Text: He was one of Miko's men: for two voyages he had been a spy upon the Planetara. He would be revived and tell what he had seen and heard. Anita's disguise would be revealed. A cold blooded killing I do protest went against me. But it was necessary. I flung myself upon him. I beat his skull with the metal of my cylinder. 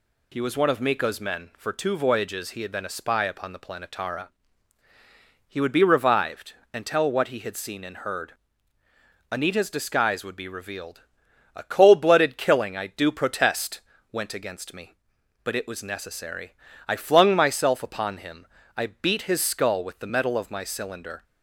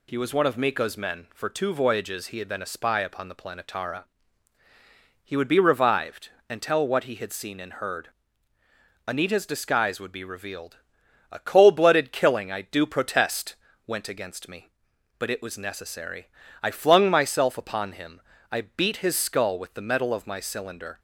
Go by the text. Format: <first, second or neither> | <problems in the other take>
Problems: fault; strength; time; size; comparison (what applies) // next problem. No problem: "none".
neither | pauses between "protest" and "went"; slight; the same in both